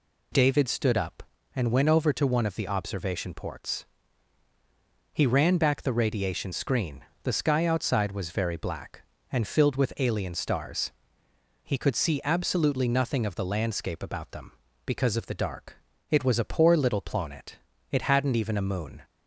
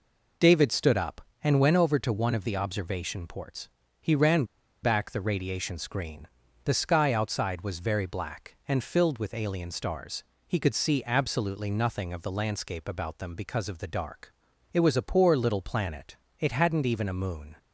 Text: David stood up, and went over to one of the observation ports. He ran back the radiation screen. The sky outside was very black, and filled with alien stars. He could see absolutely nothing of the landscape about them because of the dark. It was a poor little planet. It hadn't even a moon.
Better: first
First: none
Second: pauses between "ran" and "back"; at 4.4 s; 0.40 s long

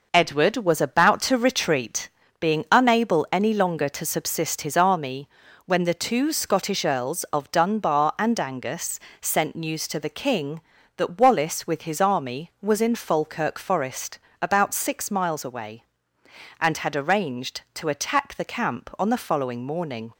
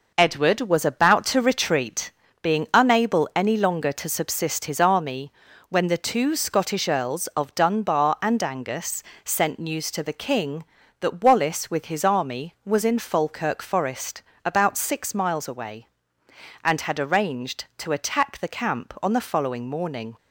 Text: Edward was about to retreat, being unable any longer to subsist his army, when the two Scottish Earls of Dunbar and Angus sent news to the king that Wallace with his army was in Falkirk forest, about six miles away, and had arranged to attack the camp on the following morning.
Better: neither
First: pauses between "Angus" and "sent"; slight; at 8.9 s; 0.20 s long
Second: pauses between "Angus" and "sent"; slight; at 9.0 s; 0.20 s long

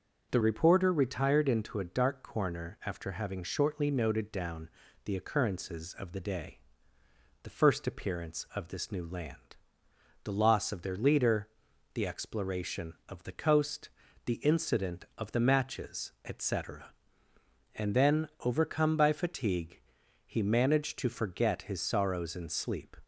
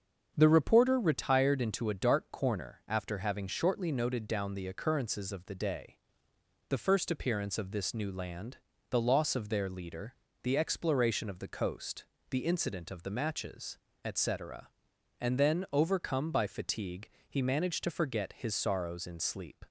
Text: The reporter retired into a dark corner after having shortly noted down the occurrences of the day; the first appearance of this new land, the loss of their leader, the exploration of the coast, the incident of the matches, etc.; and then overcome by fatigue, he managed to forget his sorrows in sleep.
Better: second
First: starts louder than the rest; until 1.3 s; 6.5 dB // changes voice at "reporter"; from 0.4 s on; 22.5 s long // pauses between "down" and "the"; slight; at 4.6 s; 0.36 s long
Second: starts louder than the rest; strong; until 1.3 s; 7 dB

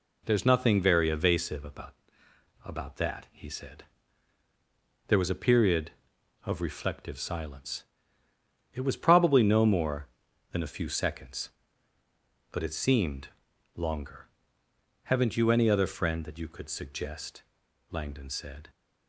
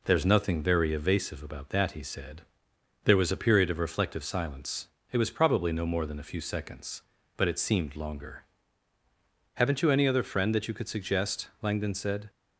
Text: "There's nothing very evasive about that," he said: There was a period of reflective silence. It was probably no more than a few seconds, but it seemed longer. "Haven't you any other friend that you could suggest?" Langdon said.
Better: second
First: says "about" twice; at 2.6 s // pauses between "seemed" and "longer"; noticeable; at 13.2 s; 0.46 s long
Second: none

